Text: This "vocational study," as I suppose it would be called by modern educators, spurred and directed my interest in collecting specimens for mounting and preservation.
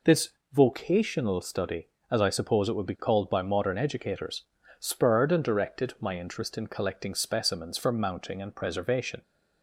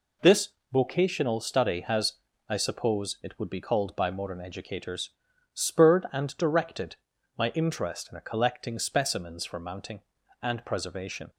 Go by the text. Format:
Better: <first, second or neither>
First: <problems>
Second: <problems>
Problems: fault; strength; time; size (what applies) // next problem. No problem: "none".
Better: first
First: pauses between "This" and "vocational"; slight; at 0.2 s; 0.24 s long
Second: pauses between "This" and "vocational"; slight; at 0.4 s; 0.24 s long // says "has" for "as"; at 1.7 s // pauses between "directed" and "my"; at 6.9 s; 0.42 s long